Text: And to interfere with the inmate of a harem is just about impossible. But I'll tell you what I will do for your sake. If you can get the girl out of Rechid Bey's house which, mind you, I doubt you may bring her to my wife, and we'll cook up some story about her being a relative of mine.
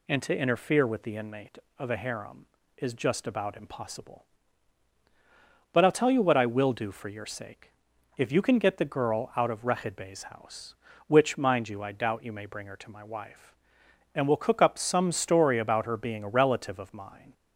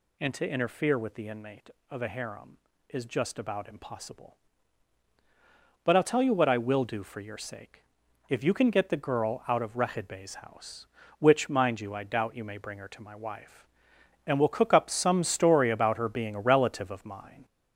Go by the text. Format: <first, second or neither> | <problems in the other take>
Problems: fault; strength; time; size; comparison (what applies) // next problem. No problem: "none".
first | gets louder; noticeable; throughout; 5 dB